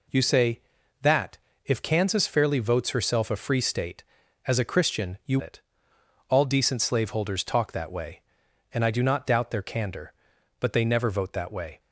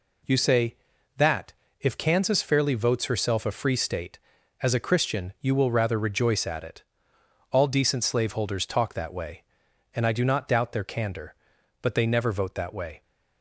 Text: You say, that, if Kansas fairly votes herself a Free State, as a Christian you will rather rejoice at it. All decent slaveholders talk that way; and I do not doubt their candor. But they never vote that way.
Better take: second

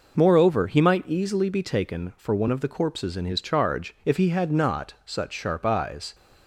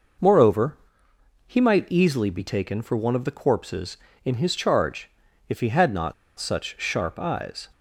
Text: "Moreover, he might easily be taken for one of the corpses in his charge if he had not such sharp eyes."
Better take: first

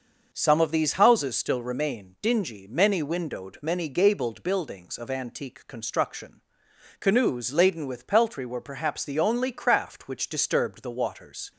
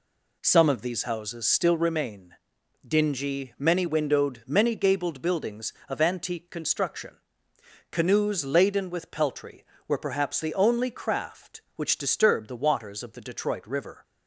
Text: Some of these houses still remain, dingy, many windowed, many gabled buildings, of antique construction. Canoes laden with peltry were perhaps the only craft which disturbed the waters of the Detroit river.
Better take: second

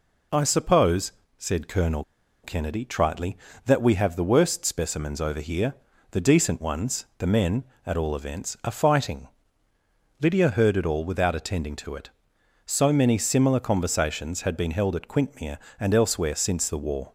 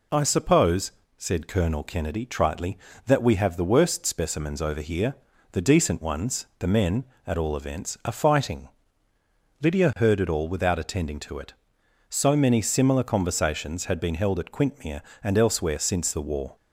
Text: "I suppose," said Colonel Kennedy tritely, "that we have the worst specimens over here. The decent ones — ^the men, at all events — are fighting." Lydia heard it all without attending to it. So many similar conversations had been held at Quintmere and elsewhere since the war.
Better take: second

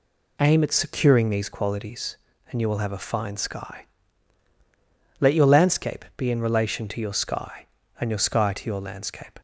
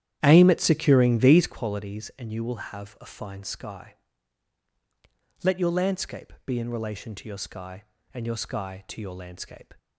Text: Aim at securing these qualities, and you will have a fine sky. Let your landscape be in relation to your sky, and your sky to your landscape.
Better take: first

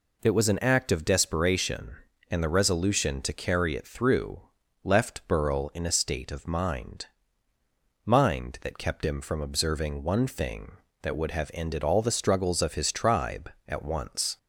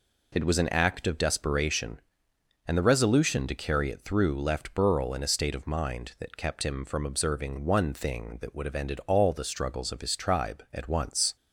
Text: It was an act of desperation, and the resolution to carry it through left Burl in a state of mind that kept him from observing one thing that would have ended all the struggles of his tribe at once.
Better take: second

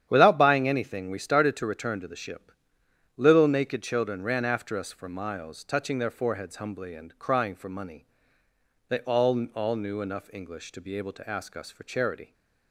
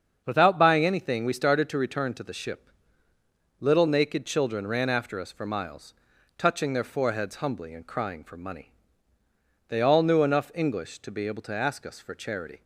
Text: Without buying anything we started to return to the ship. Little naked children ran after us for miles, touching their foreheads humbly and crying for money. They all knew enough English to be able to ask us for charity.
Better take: second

